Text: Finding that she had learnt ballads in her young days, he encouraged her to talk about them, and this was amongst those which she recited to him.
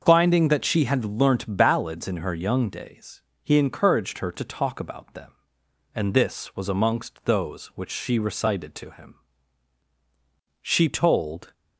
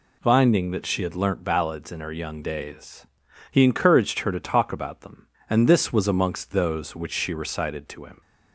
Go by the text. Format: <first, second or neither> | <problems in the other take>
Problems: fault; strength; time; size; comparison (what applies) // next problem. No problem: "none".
second | starts louder than the rest; until 1.0 s; 6.5 dB // goes on to say "She told"; noticeable; from 10.6 s on; 0.92 s long